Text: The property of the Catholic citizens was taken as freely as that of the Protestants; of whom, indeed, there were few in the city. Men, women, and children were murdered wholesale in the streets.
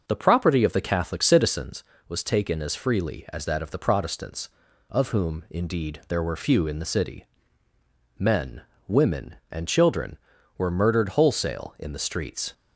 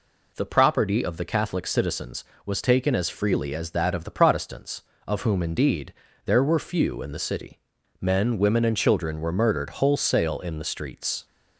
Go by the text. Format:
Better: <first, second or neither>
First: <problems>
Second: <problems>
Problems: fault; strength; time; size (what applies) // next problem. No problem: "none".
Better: second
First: starts louder than the rest; noticeable; until 1.8 s; 6 dB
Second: none